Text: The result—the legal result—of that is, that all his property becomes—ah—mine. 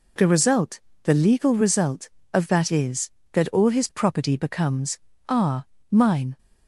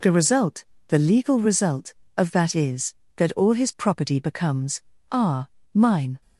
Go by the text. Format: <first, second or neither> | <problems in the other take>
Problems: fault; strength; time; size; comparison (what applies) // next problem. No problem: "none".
neither | none